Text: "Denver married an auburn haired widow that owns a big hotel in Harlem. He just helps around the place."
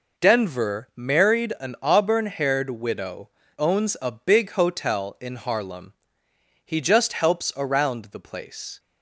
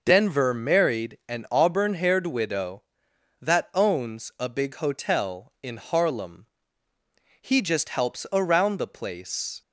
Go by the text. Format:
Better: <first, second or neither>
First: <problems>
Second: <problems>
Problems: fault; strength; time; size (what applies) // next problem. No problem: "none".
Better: second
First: skips "that"; at 3.4 s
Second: none